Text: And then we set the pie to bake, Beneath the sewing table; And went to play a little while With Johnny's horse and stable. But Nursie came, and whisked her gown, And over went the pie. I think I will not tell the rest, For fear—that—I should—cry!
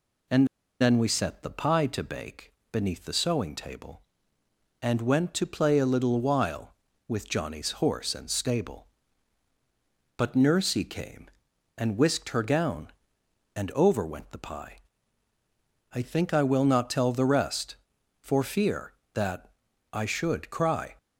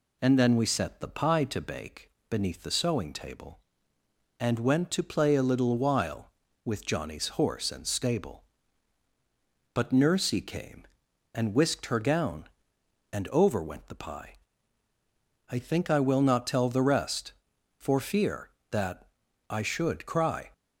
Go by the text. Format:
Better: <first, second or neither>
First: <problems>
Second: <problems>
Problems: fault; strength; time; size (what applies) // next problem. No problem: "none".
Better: second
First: pauses between "And" and "then"; slight; at 0.4 s; 0.34 s long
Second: none